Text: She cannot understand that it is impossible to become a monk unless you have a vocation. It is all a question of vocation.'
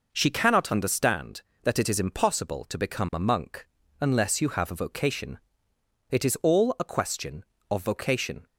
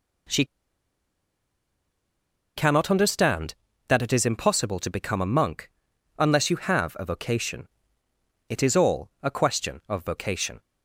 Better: first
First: pauses between "monk" and "unless"; slight; at 3.6 s; 0.34 s long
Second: pauses between "She" and "cannot"; strong; at 0.4 s; 2.1 s long // pauses between "monk" and "unless"; noticeable; at 5.6 s; 0.50 s long

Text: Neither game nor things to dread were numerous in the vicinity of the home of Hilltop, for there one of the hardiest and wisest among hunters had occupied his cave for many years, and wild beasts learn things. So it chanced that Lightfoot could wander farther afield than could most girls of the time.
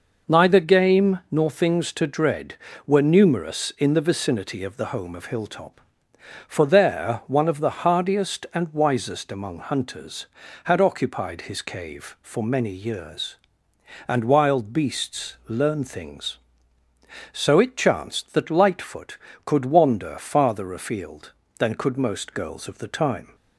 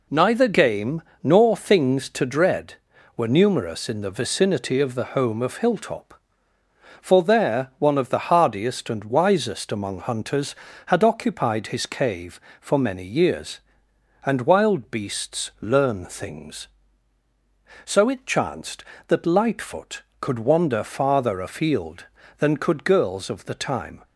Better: first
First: none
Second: pauses between "game" and "nor"; slight; at 1.0 s; 0.20 s long // skips "most"; at 22.8 s

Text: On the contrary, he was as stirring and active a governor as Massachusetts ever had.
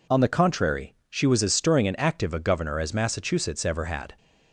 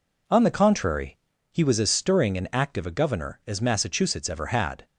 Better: second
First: says "she" for "he"; at 1.0 s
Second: none

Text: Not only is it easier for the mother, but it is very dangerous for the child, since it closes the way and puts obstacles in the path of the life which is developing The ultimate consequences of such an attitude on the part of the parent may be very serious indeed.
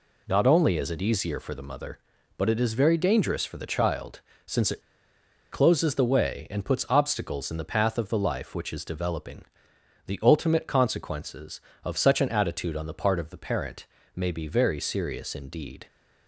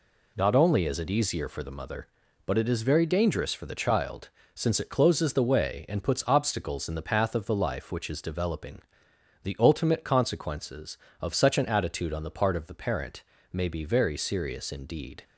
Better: second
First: pauses between "it" and "closes"; noticeable; at 4.8 s; 0.71 s long // pauses between "developing" and "The"; noticeable; at 9.4 s; 0.60 s long // pauses between "parent" and "may"; slight; at 13.8 s; 0.28 s long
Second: pauses between "developing" and "The"; noticeable; at 8.8 s; 0.60 s long // pauses between "parent" and "may"; slight; at 13.2 s; 0.28 s long

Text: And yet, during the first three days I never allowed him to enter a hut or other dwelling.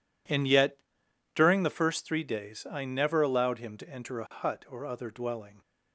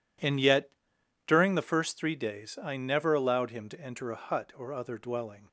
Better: neither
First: none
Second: none

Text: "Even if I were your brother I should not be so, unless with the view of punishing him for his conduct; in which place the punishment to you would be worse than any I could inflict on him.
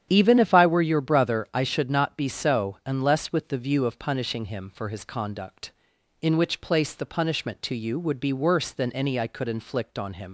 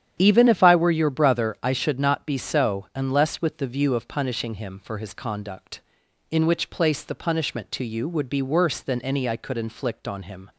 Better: second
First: starts louder than the rest; strong; until 1.1 s; 9.5 dB // leaves "him" unfinished; at 10.2 s; 80 ms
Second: starts louder than the rest; strong; until 1.2 s; 9.5 dB

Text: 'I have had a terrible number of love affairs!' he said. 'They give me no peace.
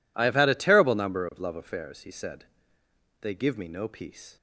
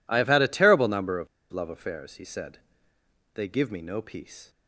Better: first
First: none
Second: pauses between "of" and "love"; slight; at 1.2 s; 0.24 s long

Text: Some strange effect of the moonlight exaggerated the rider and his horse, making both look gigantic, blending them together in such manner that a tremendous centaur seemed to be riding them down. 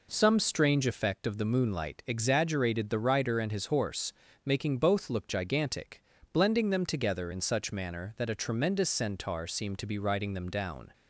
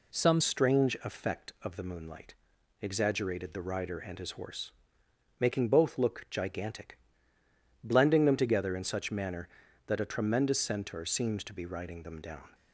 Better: first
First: none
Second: changes voice at "strange"; from 0.4 s on; 12.1 s long // pauses between "moonlight" and "exaggerated"; noticeable; at 2.3 s; 0.46 s long

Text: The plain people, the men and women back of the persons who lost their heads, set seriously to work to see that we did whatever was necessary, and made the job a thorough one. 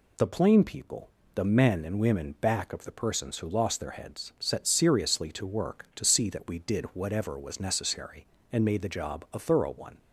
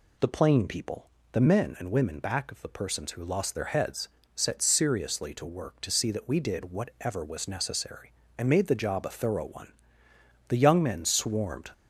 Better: first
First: none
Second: goes on to say "The young men swarmed"; noticeable; from 10.4 s on; 1.1 s long

